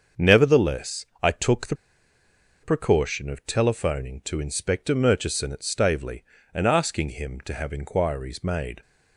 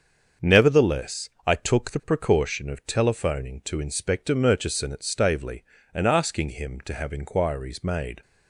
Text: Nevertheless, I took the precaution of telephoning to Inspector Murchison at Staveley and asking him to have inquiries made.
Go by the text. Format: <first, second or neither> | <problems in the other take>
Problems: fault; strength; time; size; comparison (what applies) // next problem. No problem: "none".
second | starts louder than the rest; until 1.3 s; 7 dB; also in the second // pauses between "the" and "precaution"; noticeable; at 1.7 s; 0.87 s long